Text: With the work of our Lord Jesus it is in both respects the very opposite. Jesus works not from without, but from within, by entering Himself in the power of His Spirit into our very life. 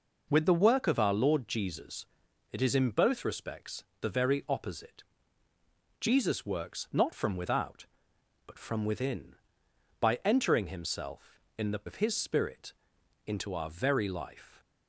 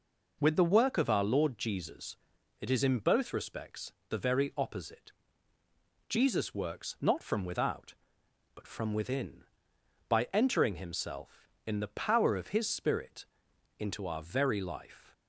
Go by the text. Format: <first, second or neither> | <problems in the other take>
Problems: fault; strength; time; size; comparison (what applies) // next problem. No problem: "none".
second | pauses between "Jesus" and "it"; noticeable; at 2.0 s; 0.48 s long; noticeable in the second // pauses between "respects" and "the"; slight; at 3.8 s; 0.18 s long; slight in the second // skips "power"; at 11.8 s // pauses between "Spirit" and "into"; noticeable; at 12.7 s; 0.54 s long; noticeable in the second